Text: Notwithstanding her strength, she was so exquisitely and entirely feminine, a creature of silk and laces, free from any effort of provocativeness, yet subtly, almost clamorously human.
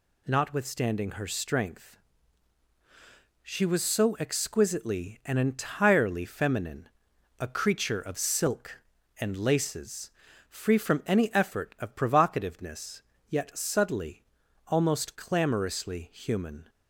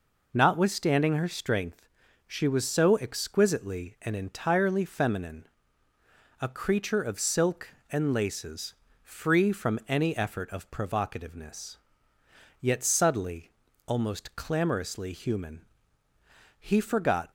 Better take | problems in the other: first | goes on to say "He forgot"; noticeable; from 16.5 s on; 0.72 s long

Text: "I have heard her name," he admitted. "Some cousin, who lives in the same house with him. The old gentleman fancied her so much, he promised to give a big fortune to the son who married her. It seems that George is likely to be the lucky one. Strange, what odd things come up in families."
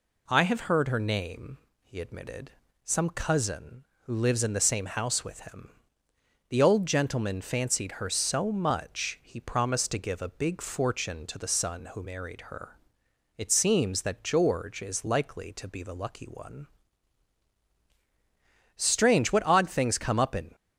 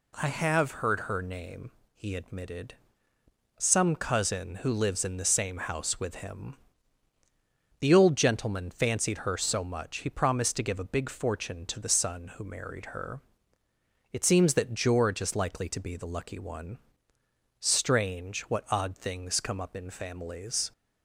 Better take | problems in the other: second | stops before "families"; at 20.5 s

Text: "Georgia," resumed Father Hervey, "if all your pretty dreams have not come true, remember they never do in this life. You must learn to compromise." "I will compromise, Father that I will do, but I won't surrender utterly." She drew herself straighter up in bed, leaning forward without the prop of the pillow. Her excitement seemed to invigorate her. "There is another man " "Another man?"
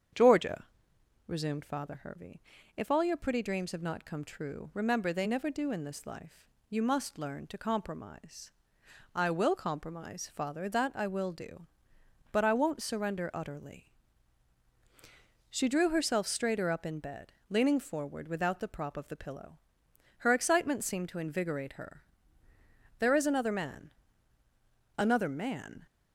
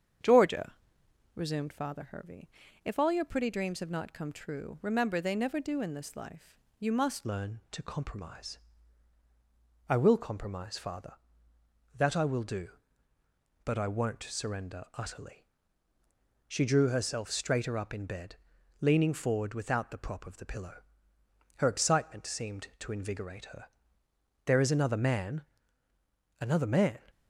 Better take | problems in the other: first | starts louder than the rest; strong; until 1.8 s; 7.5 dB; strong in the first // changes voice at "learn"; from 7.2 s on; 19.8 s long

